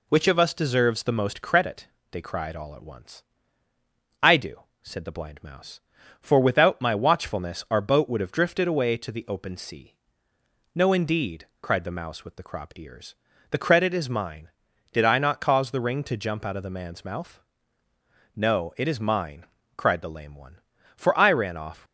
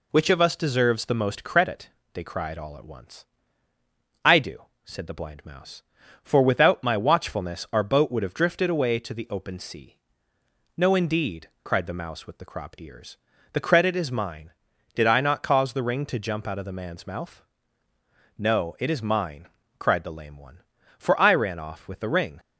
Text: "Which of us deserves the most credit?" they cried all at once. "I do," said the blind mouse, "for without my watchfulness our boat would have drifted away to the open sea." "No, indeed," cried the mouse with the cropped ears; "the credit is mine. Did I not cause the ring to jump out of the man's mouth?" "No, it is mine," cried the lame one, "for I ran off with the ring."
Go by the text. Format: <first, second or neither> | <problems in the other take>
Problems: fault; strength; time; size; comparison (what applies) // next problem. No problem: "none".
second | stops before "with the ring"; at 21.8 s